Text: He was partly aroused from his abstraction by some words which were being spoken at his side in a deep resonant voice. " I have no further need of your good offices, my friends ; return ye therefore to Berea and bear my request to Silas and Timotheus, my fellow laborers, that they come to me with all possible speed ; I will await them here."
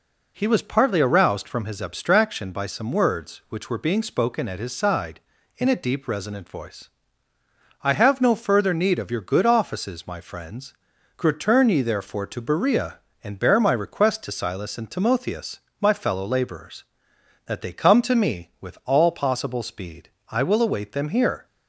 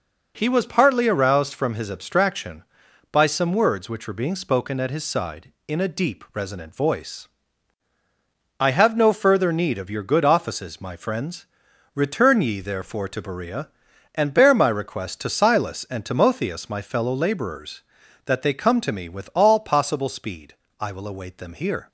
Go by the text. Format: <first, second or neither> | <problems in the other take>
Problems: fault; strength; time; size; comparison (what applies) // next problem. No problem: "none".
neither | none